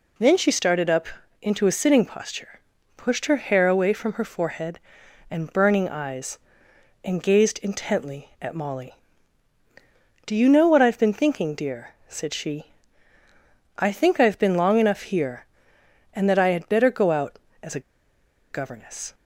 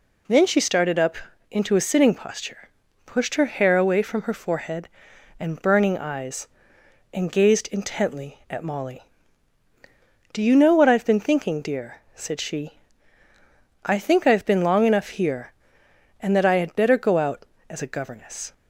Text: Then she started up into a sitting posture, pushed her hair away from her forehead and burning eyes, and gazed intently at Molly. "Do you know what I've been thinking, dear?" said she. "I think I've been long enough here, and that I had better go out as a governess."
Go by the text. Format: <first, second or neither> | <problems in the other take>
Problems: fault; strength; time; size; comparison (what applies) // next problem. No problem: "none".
second | pauses between "up" and "into"; slight; at 1.0 s; 0.34 s long; slight in the second // pauses between "a" and "governess"; noticeable; at 17.7 s; 0.70 s long